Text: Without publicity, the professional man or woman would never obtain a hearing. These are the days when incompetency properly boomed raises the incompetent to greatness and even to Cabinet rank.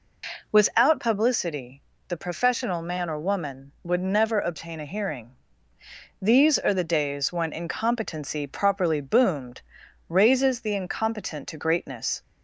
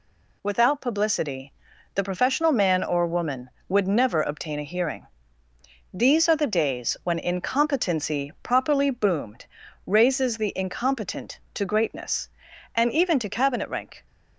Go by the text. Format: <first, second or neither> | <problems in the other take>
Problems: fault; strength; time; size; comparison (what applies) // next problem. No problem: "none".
second | pauses between "boomed" and "raises"; noticeable; at 9.6 s; 0.48 s long; also in the second // stops before "and even to Cabinet rank"; at 12.2 s